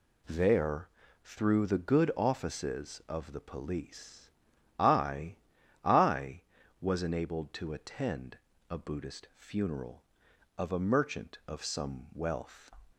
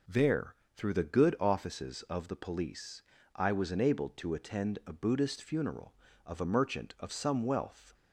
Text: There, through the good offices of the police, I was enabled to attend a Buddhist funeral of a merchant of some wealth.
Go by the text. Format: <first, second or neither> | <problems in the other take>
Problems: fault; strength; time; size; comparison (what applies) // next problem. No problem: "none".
second | says "I" twice; at 5.8 s // pauses between "attend" and "a"; slight; at 8.3 s; 0.32 s long